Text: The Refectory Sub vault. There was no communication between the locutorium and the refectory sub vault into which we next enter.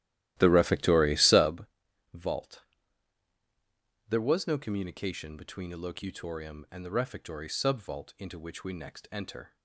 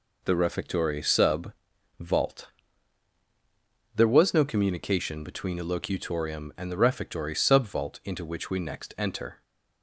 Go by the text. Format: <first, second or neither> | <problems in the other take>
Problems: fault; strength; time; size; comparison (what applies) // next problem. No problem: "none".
second | starts louder than the rest; strong; until 1.6 s; 14 dB // pauses between "Sub" and "vault"; noticeable; at 1.6 s; 0.48 s long; noticeable in the second